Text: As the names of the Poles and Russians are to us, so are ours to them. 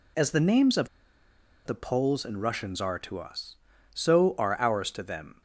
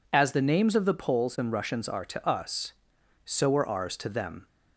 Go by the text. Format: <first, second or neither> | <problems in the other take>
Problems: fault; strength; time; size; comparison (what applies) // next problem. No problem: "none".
second | pauses between "of" and "the"; noticeable; at 0.8 s; 0.78 s long